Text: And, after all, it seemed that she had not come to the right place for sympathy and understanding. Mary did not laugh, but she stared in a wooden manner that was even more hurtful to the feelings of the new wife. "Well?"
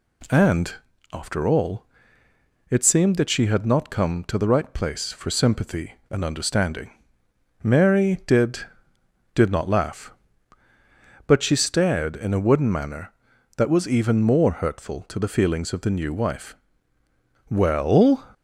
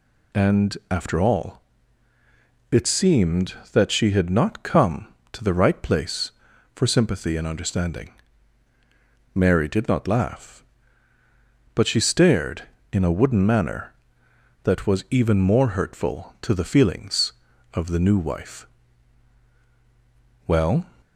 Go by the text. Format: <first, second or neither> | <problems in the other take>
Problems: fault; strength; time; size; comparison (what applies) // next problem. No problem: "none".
second | says "did" twice; at 9.3 s